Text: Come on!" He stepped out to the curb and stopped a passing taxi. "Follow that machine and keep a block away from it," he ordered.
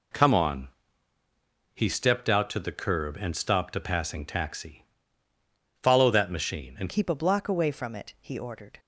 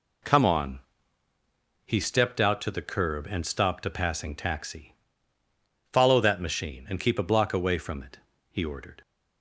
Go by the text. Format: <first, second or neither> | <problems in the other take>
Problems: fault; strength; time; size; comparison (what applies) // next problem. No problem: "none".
second | changes voice at "keep"; from 6.8 s on; 1.9 s long